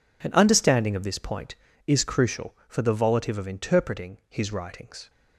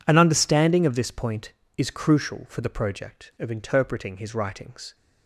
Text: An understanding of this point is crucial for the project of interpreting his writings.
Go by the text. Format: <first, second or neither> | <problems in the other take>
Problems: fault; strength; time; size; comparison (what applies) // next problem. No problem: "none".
second | says "volitive" for "project"; at 2.9 s